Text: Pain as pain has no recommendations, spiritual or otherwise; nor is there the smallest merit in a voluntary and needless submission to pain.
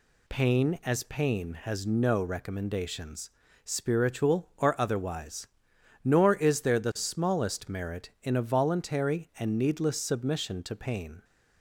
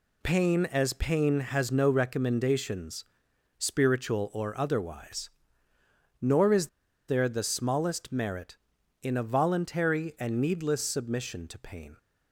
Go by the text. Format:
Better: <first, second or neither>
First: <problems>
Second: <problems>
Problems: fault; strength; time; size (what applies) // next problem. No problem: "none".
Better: first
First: none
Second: pauses between "is" and "there"; at 6.6 s; 0.41 s long